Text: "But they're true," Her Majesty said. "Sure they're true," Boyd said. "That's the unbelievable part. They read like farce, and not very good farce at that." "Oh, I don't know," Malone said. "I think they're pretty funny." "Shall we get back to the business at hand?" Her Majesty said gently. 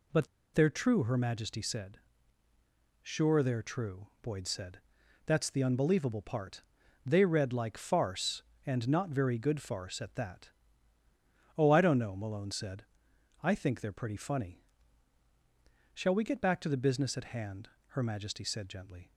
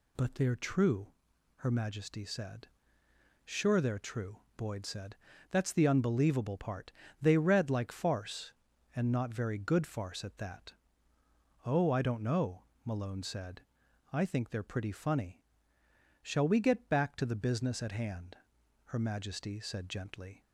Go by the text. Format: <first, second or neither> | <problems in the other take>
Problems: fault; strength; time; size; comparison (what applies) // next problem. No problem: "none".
second | pauses between "But" and "they're"; slight; at 0.2 s; 0.26 s long